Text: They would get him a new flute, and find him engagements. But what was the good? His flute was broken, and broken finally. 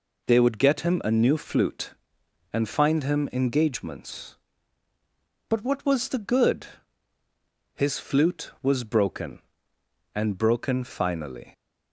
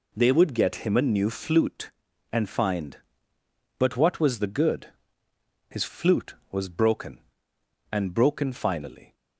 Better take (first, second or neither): first